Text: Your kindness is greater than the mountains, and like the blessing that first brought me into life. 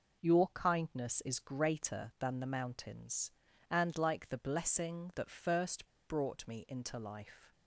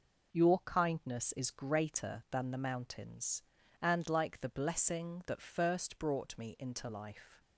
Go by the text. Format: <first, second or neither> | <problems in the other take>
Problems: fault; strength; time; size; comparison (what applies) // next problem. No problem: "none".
second | pauses between "first" and "brought"; slight; at 5.8 s; 0.20 s long